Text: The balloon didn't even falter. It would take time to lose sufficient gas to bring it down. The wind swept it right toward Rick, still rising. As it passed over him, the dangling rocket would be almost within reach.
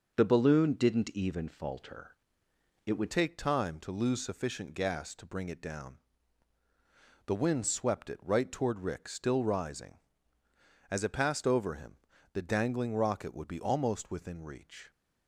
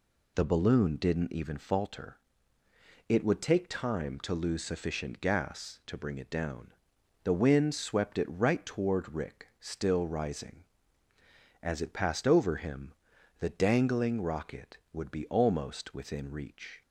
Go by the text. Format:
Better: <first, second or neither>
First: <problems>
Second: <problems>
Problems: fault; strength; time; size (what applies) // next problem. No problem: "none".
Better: second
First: changes voice at "take"; from 3.1 s on; 11.8 s long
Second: none